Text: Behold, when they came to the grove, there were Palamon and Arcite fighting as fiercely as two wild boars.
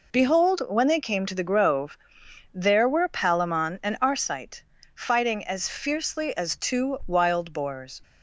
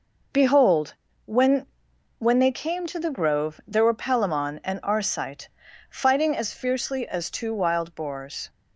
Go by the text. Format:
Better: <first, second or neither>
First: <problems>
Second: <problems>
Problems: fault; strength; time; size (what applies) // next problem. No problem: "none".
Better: first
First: pauses between "Arcite" and "fighting"; slight; at 4.6 s; 0.32 s long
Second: says "when" twice; at 2.1 s // pauses between "Arcite" and "fighting"; at 5.4 s; 0.40 s long